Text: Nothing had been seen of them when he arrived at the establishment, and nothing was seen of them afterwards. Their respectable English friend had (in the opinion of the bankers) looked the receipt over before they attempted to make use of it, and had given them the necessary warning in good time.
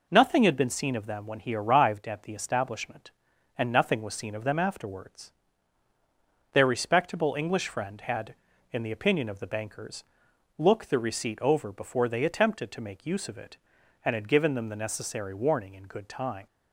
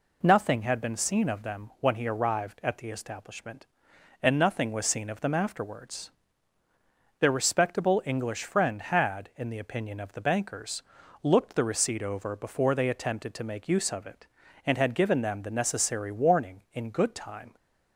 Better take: neither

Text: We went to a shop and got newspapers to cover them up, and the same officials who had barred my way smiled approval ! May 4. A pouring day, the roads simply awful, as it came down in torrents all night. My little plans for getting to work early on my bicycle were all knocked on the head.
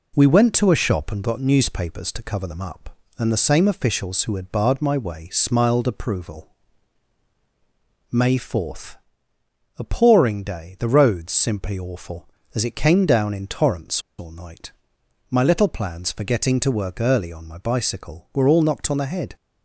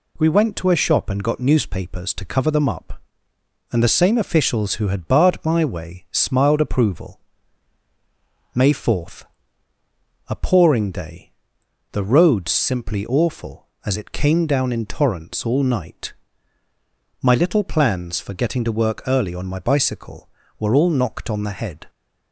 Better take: second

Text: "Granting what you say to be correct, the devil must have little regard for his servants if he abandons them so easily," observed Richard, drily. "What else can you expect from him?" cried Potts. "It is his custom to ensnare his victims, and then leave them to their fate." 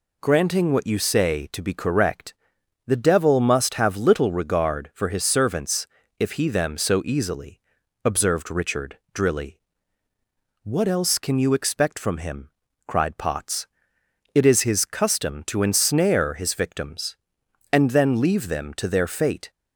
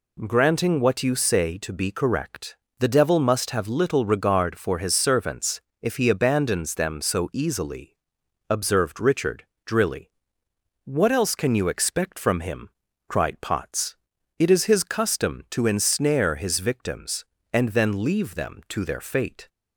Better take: second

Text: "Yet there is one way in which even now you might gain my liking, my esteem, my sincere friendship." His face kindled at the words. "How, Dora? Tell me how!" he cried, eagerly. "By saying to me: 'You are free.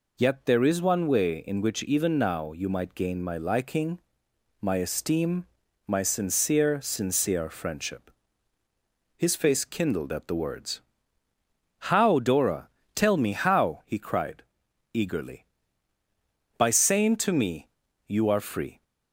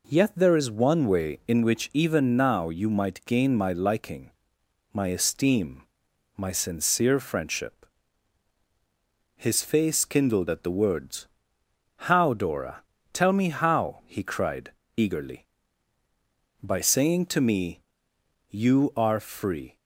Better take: second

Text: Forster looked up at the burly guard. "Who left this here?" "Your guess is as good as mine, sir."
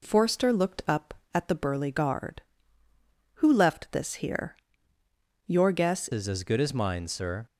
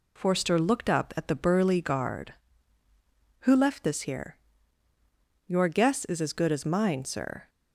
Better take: second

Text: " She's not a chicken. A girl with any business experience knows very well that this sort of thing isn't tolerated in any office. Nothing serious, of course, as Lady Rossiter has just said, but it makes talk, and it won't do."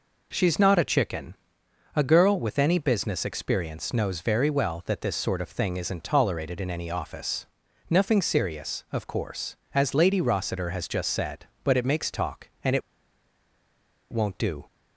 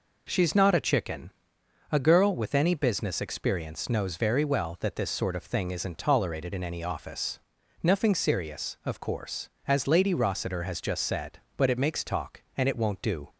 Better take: second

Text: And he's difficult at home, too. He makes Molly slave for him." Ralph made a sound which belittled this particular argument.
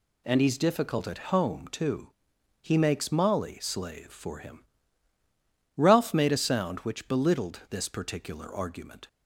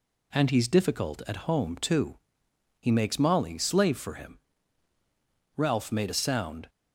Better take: first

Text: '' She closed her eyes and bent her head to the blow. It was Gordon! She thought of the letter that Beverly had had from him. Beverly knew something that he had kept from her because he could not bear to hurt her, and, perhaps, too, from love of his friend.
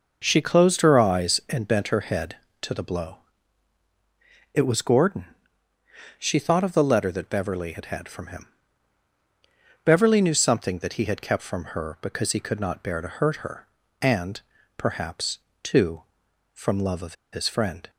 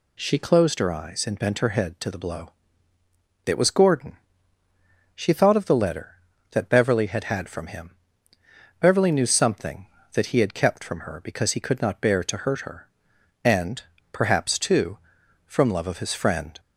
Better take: second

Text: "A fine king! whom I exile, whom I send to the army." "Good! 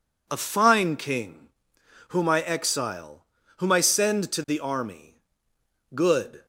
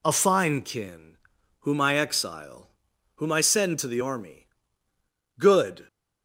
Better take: first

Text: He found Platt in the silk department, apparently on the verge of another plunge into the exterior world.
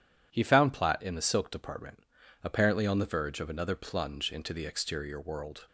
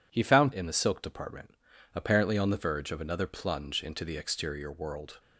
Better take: first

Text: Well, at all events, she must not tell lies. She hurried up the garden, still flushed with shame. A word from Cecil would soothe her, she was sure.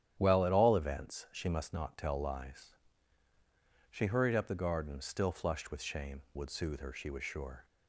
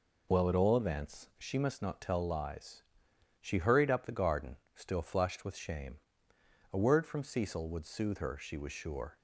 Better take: second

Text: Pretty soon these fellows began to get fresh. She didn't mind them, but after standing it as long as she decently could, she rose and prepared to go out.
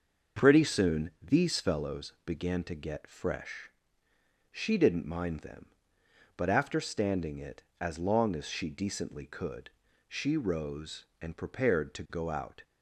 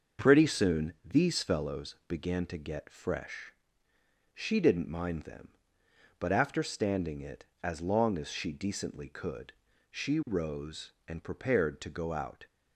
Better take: neither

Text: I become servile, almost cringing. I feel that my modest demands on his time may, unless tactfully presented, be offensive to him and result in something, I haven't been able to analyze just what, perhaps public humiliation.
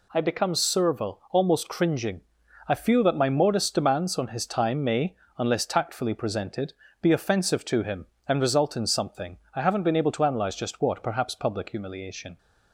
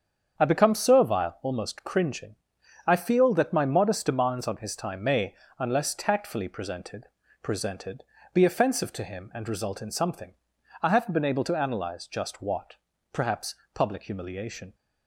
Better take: first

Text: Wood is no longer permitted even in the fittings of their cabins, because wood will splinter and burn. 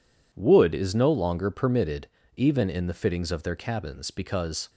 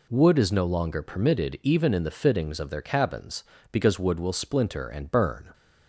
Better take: second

